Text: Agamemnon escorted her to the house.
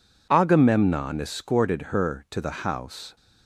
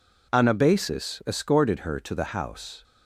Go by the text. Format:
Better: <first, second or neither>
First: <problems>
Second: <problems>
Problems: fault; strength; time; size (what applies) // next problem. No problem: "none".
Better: first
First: none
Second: says "Anabasis" for "Agamemnon"; at 0.3 s